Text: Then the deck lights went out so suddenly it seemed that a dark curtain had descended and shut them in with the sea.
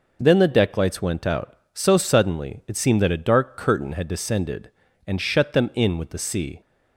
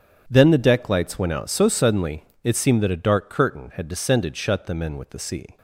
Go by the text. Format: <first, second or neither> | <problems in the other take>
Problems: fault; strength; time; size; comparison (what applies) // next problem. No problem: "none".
first | starts louder than the rest; strong; until 1.2 s; 8.5 dB // pauses between "suddenly" and "it"; slight; at 2.2 s; 0.18 s long // skips "and"; at 4.3 s